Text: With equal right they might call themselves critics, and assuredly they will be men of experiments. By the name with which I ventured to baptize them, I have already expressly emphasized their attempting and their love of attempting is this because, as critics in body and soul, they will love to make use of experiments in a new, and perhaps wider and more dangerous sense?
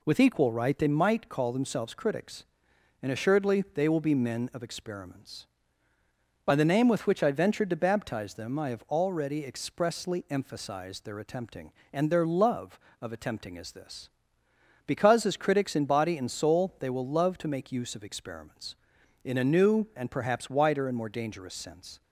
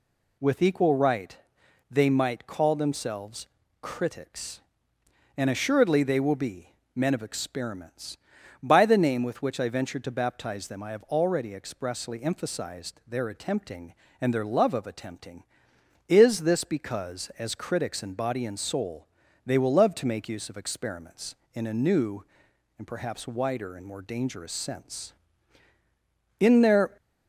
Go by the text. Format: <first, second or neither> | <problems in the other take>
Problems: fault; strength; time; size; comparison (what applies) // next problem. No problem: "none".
first | pauses between "right" and "they"; noticeable; at 1.3 s; 0.54 s long // pauses between "themselves" and "critics"; slight; at 3.4 s; 0.34 s long // pauses between "be" and "men"; slight; at 6.7 s; 0.22 s long // goes on to say "In their"; from 26.3 s on; 0.58 s long